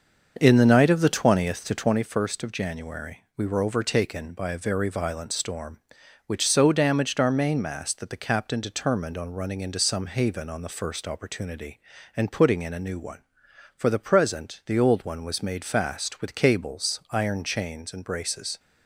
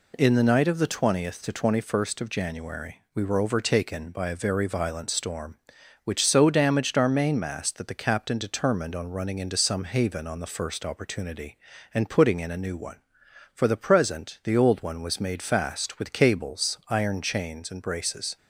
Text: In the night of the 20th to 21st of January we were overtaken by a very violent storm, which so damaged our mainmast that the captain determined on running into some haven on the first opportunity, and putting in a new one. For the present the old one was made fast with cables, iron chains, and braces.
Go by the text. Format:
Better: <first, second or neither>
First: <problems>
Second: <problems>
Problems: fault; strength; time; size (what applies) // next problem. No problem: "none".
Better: second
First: starts louder than the rest; until 2.0 s; 6.5 dB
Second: none